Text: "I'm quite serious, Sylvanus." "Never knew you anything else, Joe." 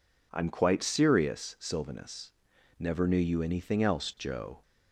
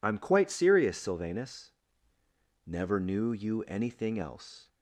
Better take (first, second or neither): first